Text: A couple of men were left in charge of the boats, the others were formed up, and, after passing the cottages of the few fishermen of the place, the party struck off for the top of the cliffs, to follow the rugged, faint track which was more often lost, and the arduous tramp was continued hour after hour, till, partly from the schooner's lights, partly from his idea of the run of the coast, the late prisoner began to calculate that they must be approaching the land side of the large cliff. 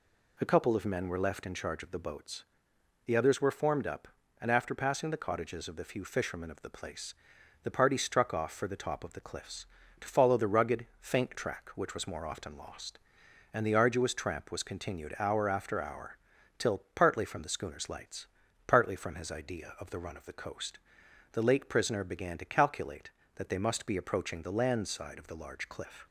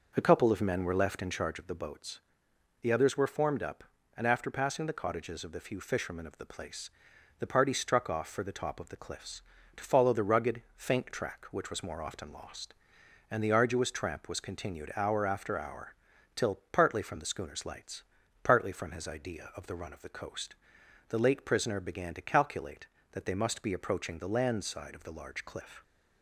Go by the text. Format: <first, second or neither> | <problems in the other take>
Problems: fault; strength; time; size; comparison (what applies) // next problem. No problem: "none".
first | starts louder than the rest; noticeable; until 1.6 s; 5 dB